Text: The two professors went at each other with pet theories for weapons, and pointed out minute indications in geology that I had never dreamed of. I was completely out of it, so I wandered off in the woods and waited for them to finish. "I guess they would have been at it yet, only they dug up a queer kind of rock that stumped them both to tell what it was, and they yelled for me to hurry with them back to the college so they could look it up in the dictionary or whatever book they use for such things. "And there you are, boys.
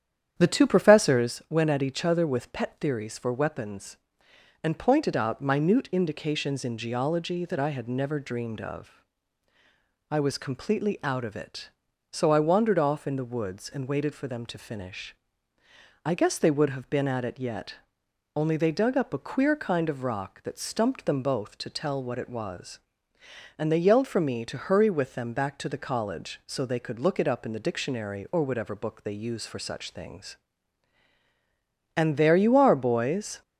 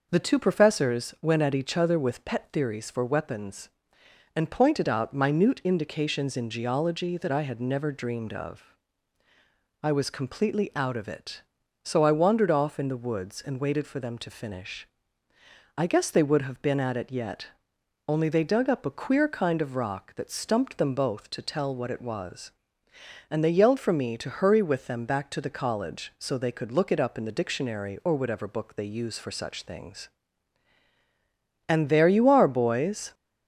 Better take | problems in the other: second | starts louder than the rest; strong; until 1.3 s; 9 dB

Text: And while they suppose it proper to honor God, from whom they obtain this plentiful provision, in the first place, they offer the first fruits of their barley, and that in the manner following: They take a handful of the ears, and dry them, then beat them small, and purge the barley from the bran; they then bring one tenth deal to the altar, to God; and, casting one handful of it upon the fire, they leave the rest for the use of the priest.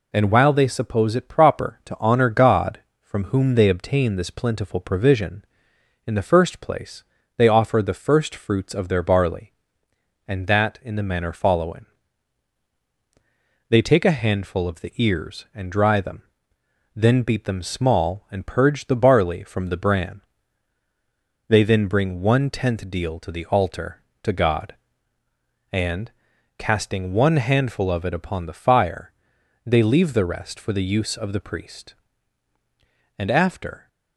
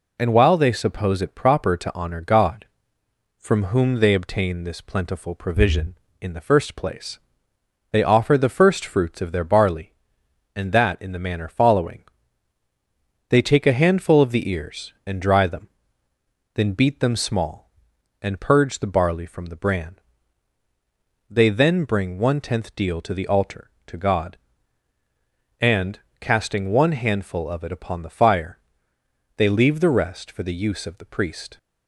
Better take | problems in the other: second | goes on to say "And after"; noticeable; from 33.1 s on; 0.70 s long

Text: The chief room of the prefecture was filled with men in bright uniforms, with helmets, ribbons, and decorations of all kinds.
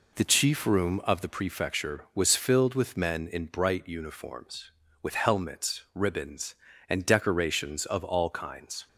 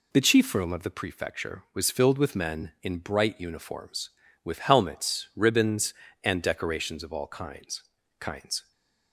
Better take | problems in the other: first | says "kinds" twice; at 8.1 s // stays silent after the last word; slight; from 8.6 s on; 0.5 s long

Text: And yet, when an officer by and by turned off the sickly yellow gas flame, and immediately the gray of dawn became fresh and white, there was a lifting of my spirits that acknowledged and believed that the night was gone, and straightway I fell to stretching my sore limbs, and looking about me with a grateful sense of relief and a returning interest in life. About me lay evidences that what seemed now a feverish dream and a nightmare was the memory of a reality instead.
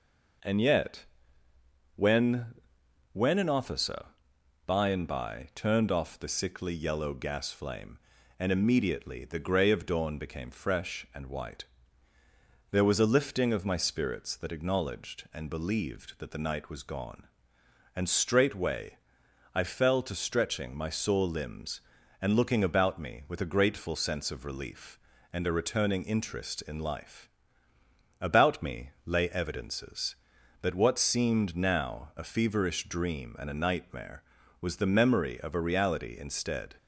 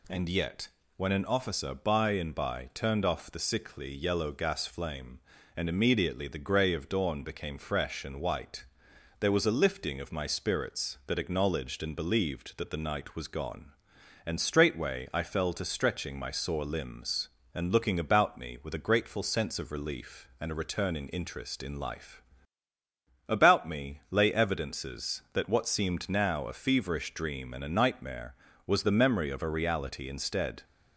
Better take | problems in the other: second | says "when" twice; at 3.1 s // pauses between "straightway" and "I"; noticeable; at 18.9 s; 0.56 s long

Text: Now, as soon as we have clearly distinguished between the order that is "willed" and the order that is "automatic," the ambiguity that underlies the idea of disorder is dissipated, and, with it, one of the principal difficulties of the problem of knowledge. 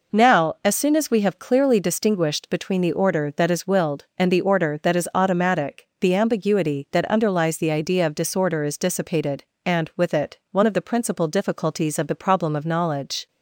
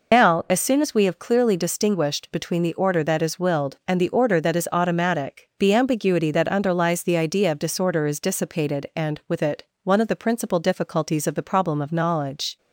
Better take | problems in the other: first | loses the start of "Now"; at 0.1 s; 115 ms

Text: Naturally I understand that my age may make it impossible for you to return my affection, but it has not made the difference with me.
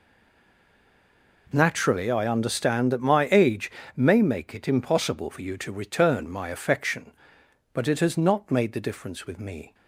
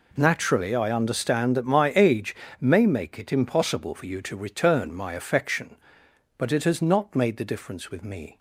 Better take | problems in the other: second | stays silent before the first word; noticeable; until 1.4 s; 1.4 s long // pauses between "age" and "may"; slight; at 3.7 s; 0.24 s long; slight in the second

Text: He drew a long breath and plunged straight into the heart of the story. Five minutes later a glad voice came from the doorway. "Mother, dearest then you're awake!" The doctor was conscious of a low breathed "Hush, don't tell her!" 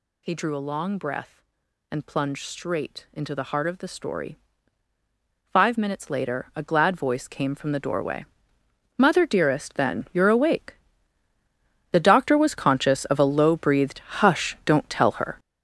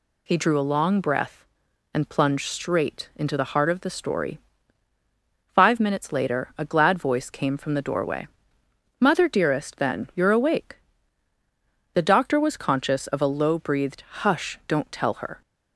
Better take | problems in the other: second | gets louder; strong; throughout; 9.5 dB // pauses between "breathed" and "Hush"; slight; at 13.9 s; 0.22 s long; slight in the second

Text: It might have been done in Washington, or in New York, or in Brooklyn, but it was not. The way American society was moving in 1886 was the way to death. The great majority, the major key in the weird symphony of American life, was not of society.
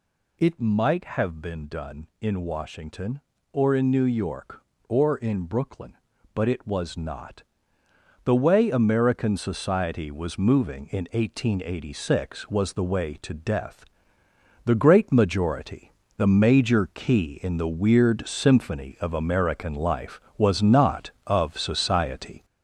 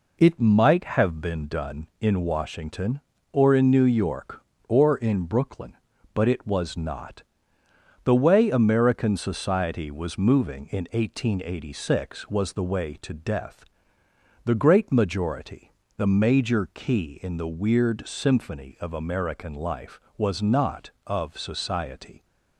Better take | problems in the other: second | gets louder; noticeable; throughout; 5.5 dB

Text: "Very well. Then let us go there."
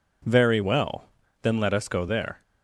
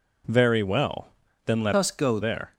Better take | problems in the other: first | changes voice from "us" to "go"; from 1.7 to 2.1 s; 0.4 s long

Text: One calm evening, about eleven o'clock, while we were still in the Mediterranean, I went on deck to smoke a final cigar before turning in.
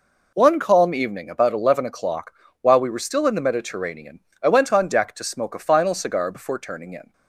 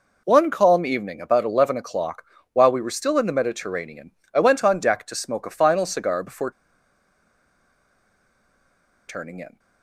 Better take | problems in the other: first | pauses between "before" and "turning"; strong; at 6.5 s; 2.5 s long

